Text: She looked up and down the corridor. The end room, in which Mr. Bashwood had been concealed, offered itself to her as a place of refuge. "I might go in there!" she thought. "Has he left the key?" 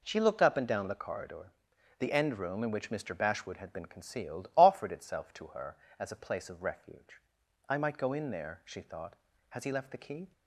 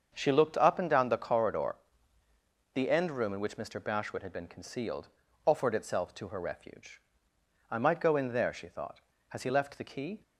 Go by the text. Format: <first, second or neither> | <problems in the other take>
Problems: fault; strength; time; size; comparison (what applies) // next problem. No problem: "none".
first | starts louder than the rest; until 1.1 s; 7 dB // skips "as a place of"; at 6.3 s